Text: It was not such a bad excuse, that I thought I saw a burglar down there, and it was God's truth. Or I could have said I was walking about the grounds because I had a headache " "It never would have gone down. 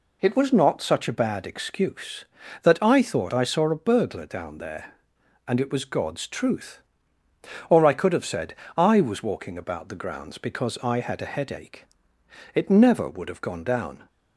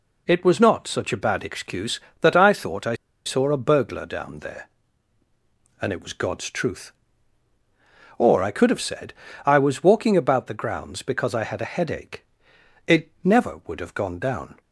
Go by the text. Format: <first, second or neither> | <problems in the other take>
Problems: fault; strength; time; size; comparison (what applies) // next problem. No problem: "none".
first | pauses between "I" and "saw"; slight; at 2.9 s; 0.30 s long // pauses between "said" and "I"; slight; at 9.1 s; 0.32 s long; slight in the first